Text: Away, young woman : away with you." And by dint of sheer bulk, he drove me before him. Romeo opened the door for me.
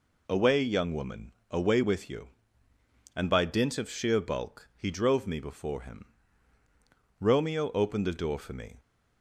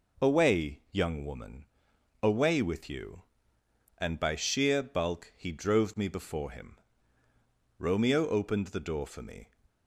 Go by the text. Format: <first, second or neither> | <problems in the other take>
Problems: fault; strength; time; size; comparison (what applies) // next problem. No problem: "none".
first | skips "dint of"; at 4.3 s